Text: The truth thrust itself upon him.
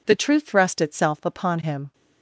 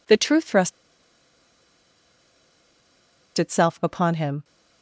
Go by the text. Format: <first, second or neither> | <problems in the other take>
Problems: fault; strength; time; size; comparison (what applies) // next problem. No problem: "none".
first | pauses between "thrust" and "itself"; strong; at 0.7 s; 2.6 s long